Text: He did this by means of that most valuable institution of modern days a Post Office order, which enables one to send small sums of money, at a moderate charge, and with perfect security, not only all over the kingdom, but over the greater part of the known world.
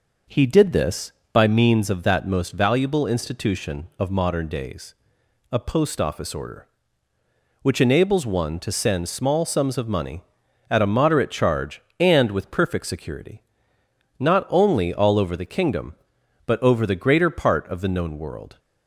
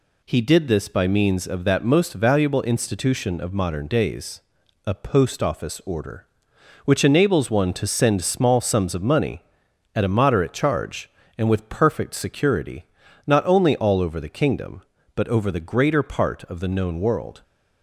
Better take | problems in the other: second | starts louder than the rest; noticeable; until 1.5 s; 5.5 dB // pauses between "days" and "a"; noticeable; at 4.9 s; 0.58 s long; also in the second

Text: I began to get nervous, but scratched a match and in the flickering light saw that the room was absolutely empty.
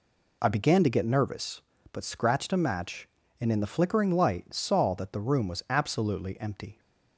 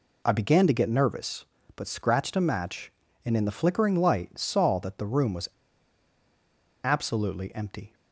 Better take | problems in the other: first | pauses between "was" and "absolutely"; strong; at 5.4 s; 1.3 s long

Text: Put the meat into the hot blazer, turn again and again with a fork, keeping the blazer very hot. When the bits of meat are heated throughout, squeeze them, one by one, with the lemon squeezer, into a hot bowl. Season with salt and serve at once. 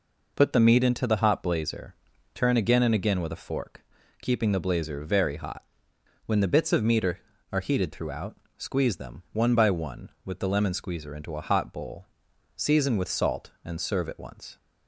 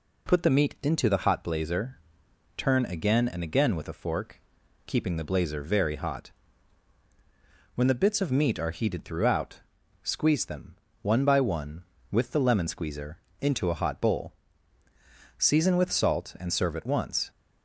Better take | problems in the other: second | says "are" twice; at 7.5 s

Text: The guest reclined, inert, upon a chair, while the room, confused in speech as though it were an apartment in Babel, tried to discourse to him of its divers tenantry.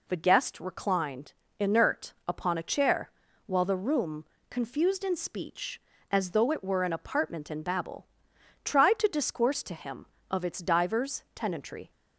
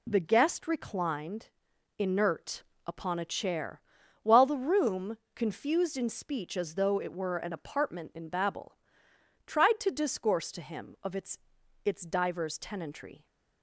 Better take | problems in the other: first | says "its" twice; at 11.8 s

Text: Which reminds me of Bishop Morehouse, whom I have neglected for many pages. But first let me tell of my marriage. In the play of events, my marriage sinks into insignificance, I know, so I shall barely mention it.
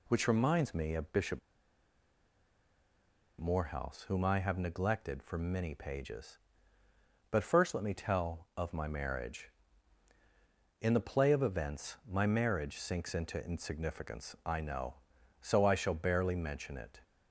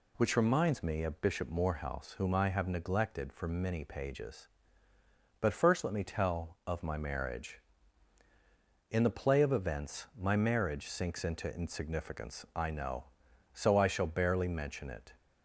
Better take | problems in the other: second | pauses between "Bishop" and "Morehouse"; strong; at 1.3 s; 2.0 s long

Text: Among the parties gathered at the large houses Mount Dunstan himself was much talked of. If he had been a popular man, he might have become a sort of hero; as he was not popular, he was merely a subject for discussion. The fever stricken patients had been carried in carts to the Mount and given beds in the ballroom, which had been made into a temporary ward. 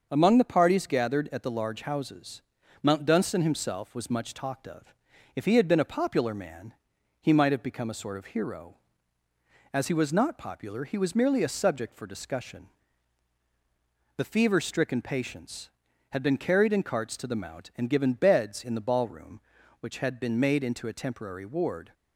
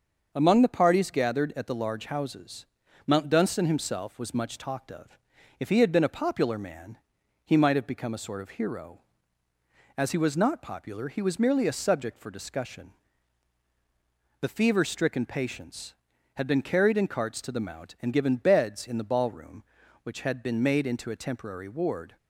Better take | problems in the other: neither | starts louder than the rest; the same in both // pauses between "houses" and "Mount"; the same in both

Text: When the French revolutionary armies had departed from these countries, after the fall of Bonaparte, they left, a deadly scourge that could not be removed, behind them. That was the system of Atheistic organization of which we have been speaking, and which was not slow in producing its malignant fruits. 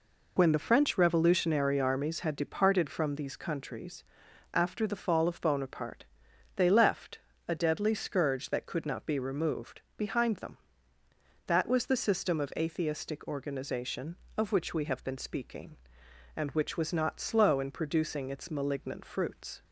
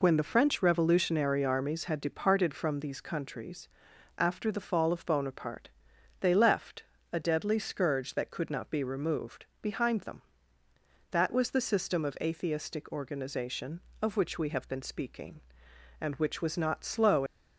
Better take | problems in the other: first | stops before "in producing its malignant fruits"; at 17.2 s

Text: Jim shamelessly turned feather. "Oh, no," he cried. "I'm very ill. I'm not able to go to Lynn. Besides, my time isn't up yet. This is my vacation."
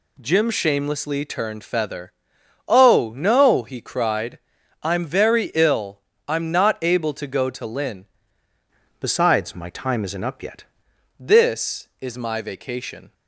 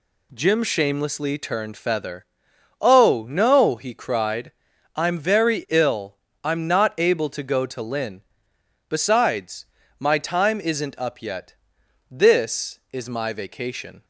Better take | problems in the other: second | changes voice from "Besides" to "yet"; from 8.9 to 10.6 s; 1.7 s long

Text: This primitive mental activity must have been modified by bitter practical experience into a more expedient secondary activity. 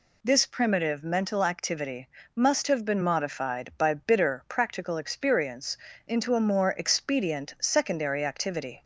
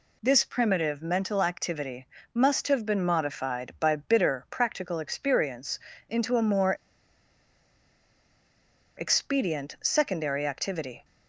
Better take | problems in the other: first | pauses between "activity" and "must"; slight; at 2.0 s; 0.30 s long; slight in the first // pauses between "experience" and "into"; slight; at 5.7 s; 0.30 s long; slight in the first // pauses between "more" and "expedient"; strong; at 6.7 s; 2.2 s long

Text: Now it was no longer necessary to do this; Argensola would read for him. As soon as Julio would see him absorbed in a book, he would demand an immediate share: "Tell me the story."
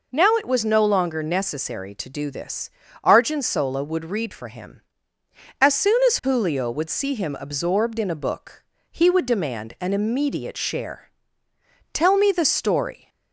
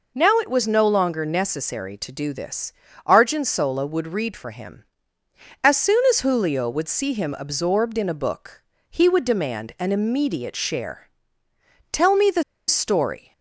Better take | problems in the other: first | pauses between "the" and "story"; slight; at 12.4 s; 0.24 s long

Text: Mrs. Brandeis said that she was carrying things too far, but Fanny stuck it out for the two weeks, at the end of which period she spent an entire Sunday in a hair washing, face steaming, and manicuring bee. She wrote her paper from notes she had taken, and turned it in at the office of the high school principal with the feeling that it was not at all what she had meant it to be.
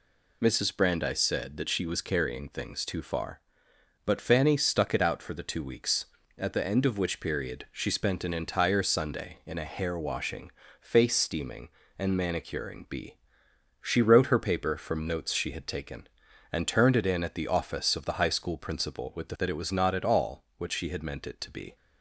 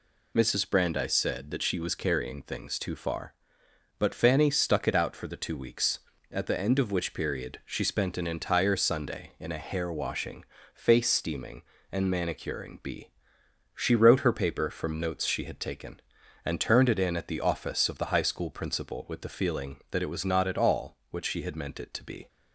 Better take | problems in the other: second | skips "feeling"; at 19.3 s

